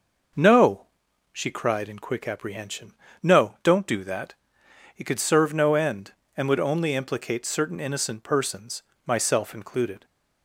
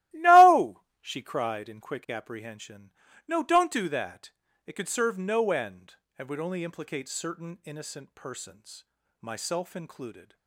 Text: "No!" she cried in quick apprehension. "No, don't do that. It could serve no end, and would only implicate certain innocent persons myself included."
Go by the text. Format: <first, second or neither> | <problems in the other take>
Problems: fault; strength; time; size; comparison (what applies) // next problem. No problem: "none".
first | starts louder than the rest; strong; until 1.7 s; 15.5 dB // pauses between "persons" and "myself"; at 8.8 s; 0.38 s long; slight in the first